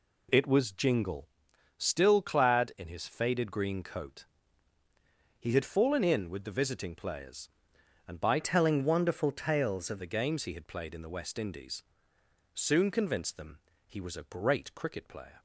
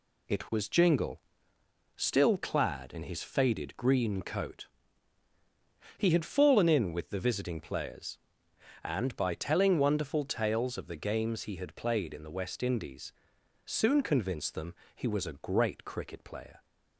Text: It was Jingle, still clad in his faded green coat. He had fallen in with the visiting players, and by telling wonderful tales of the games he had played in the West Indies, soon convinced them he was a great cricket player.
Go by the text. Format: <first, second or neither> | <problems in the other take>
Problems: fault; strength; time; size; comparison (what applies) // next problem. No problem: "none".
second | changes voice from "telling" to "of"; from 8.3 to 10.0 s; 1.7 s long // pauses between "them" and "he"; slight; at 13.5 s; 0.26 s long; slight in the second